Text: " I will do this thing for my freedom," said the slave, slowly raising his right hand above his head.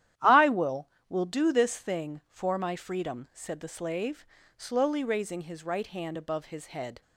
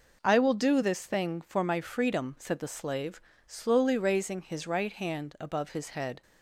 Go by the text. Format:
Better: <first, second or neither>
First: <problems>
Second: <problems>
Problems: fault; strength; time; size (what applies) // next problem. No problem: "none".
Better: second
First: starts louder than the rest; strong; until 1.4 s; 11.5 dB // says "will" twice; at 1.0 s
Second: none